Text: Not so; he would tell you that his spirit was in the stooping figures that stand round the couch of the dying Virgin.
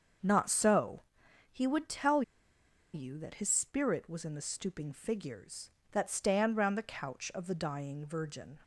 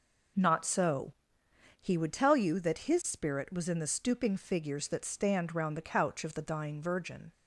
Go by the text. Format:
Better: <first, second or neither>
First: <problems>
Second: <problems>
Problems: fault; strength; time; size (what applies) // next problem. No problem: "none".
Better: second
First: starts louder than the rest; until 1.6 s; 6.5 dB // pauses between "tell" and "you"; noticeable; at 2.2 s; 0.72 s long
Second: none